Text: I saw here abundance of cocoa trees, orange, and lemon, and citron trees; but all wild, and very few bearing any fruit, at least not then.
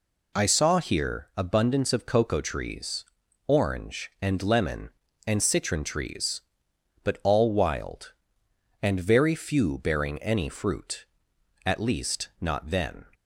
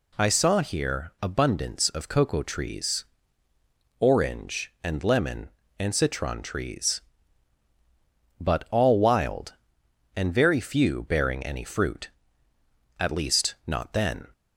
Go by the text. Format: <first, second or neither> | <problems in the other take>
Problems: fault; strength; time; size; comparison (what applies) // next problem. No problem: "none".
neither | none